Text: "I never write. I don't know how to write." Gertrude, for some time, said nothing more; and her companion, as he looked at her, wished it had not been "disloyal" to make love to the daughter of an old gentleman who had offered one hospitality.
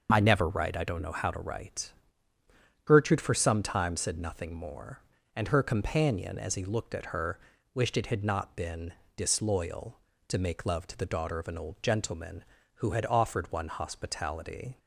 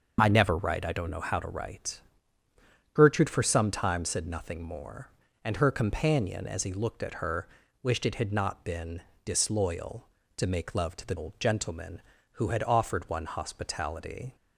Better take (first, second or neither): first